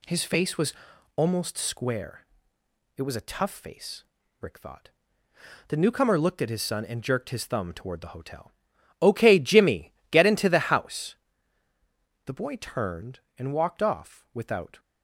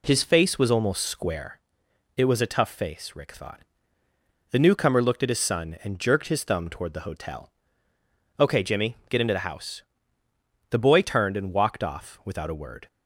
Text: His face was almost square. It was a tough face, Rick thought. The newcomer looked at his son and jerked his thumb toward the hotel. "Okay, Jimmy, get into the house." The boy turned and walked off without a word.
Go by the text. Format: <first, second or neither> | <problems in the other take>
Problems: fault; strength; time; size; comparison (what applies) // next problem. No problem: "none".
second | pauses between "was" and "almost"; at 0.7 s; 0.42 s long // stops before "a word"; at 14.7 s